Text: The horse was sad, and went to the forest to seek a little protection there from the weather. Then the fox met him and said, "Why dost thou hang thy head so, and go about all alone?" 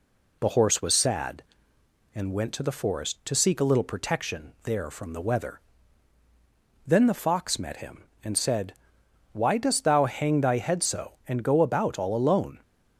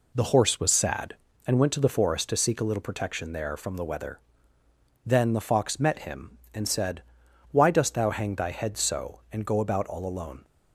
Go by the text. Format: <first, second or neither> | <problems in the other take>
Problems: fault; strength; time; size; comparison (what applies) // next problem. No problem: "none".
neither | none